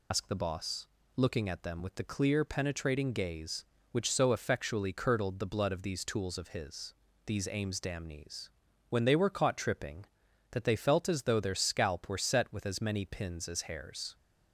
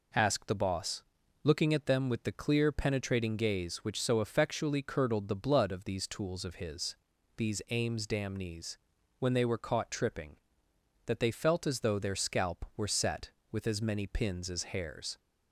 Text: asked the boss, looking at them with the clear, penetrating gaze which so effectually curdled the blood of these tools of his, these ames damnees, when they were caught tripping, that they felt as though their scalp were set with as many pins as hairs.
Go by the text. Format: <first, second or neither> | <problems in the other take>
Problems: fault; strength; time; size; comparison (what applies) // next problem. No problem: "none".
second | loses the start of "asked"; at 0.1 s; 90 ms